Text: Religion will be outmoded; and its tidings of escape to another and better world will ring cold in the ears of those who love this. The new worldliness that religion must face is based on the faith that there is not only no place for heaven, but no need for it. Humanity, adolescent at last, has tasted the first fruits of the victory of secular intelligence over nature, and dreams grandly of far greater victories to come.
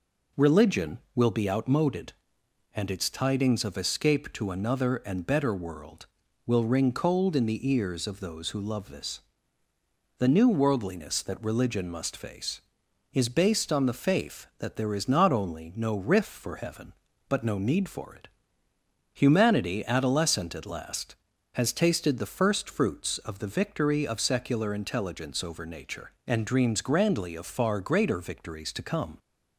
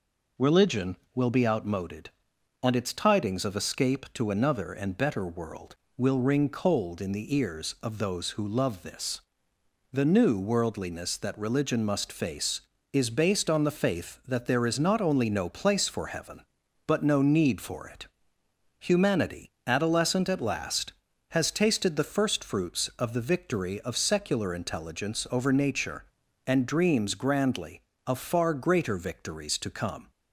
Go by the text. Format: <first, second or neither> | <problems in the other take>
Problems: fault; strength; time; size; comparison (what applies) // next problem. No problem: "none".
second | says "riff" for "place"; at 15.9 s